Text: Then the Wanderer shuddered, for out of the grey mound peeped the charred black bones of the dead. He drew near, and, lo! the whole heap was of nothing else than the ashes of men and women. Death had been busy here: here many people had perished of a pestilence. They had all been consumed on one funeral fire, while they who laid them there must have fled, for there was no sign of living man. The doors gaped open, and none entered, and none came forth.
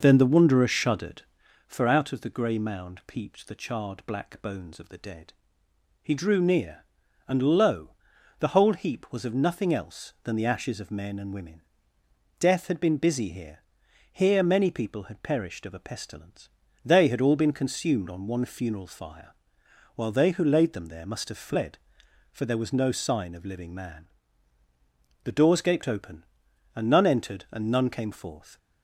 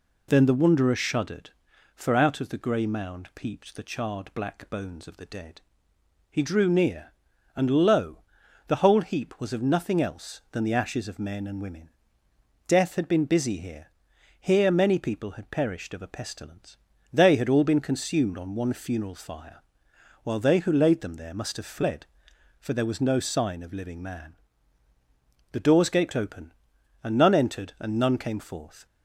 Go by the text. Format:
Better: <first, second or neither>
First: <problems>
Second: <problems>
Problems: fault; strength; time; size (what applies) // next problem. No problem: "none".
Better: second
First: starts louder than the rest; noticeable; until 1.5 s; 5.5 dB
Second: none